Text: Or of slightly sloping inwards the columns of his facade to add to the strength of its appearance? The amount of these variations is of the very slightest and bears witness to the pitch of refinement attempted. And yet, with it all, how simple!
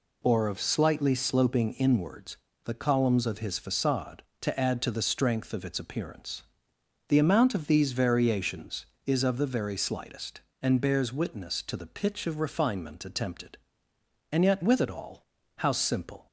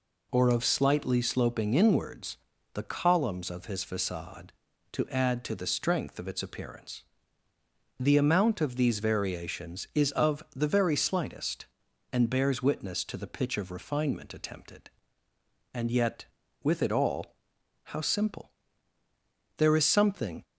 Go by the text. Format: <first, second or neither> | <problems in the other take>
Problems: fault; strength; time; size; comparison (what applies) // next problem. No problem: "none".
first | pauses between "inwards" and "the"; at 2.3 s; 0.38 s long; slight in the first // goes on to say "There is something"; noticeable; from 19.5 s on; 0.86 s long